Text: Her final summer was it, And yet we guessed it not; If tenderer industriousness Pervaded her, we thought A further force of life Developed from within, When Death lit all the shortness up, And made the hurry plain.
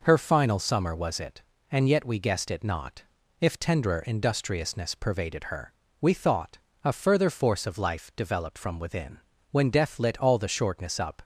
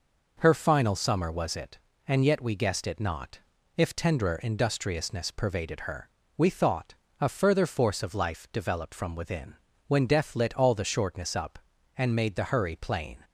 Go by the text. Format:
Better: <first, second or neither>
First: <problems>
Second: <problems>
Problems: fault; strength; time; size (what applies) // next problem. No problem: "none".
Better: second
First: pauses between "thought" and "A"; slight; at 6.5 s; 0.26 s long // stops before "And made the hurry plain"; at 11.2 s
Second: pauses between "thought" and "A"; slight; at 6.9 s; 0.26 s long